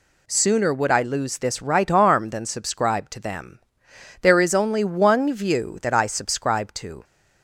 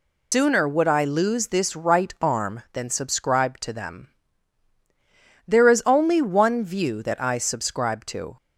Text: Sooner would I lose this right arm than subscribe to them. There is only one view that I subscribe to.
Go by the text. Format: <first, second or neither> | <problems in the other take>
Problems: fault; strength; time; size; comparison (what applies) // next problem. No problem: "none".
first | loses the start of "Sooner"; at 0.3 s; 155 ms